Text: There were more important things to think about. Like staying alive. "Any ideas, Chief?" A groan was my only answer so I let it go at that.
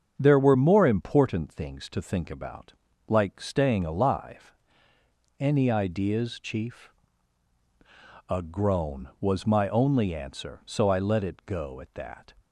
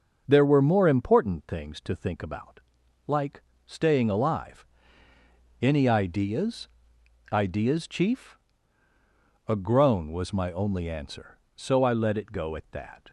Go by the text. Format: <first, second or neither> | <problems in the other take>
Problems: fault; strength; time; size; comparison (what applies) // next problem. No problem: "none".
first | starts louder than the rest; until 1.2 s; 6.5 dB; also in the first // pauses between "Like" and "staying"; slight; at 3.4 s; 0.24 s long // says "ideas" twice; at 7.2 s